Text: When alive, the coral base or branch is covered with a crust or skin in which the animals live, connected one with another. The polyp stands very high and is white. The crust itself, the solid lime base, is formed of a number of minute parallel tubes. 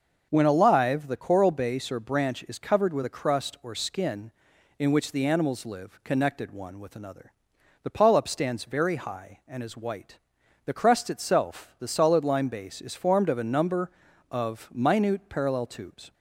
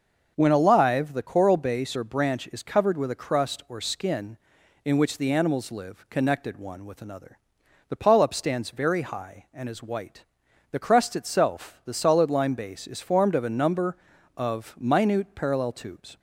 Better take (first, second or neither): neither